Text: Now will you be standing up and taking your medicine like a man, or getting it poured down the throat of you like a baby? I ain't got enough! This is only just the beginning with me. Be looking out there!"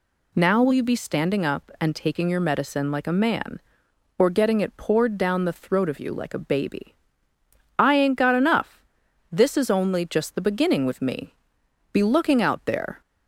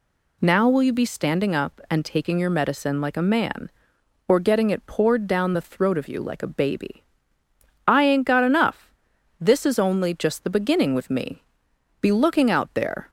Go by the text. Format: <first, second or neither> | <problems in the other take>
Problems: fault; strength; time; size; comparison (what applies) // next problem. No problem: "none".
neither | none